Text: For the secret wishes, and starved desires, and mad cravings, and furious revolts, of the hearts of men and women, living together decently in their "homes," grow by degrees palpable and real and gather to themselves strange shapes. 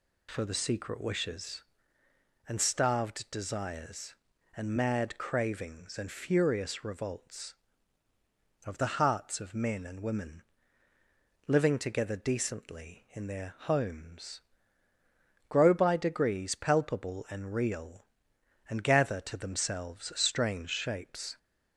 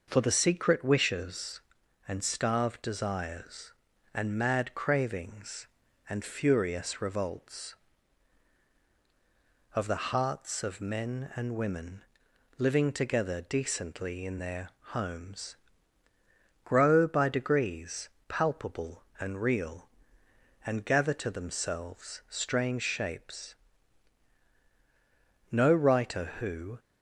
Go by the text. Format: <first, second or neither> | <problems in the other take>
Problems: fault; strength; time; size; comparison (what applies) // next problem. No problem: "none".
first | pauses between "their" and "homes"; slight; at 14.6 s; 0.26 s long // pauses between "degrees" and "palpable"; slight; at 18.0 s; 0.22 s long // goes on to say "No writer who"; noticeable; from 25.5 s on; 1.2 s long